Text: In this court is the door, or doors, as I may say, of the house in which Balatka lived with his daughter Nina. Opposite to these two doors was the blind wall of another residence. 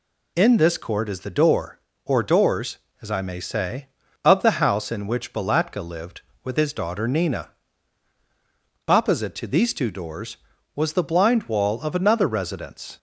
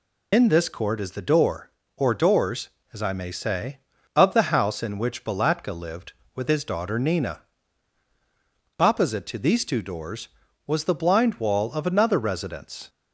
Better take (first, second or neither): first